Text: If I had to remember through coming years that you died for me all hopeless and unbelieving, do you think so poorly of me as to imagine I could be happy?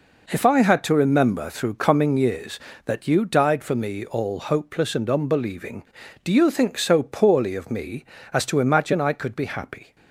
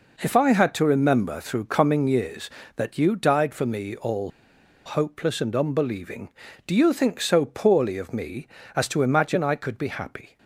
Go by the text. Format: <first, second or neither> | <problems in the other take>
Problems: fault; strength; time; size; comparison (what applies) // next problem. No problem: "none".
first | pauses between "all" and "hopeless"; noticeable; at 4.3 s; 0.55 s long